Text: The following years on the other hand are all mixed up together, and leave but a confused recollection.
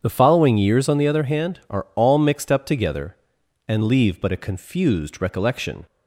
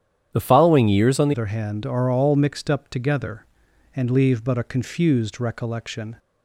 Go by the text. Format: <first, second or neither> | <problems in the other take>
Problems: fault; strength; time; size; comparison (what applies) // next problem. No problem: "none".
first | starts louder than the rest; strong; until 1.3 s; 10 dB; strong in the first // changes voice at "other"; from 1.3 s on; 4.8 s long